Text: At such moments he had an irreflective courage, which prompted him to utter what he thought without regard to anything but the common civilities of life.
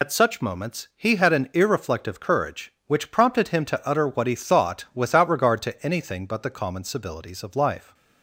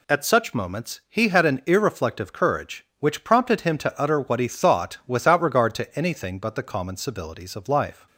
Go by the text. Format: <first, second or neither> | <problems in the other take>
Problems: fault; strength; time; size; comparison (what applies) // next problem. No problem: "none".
second | loses the start of "At"; at 0.0 s; 75 ms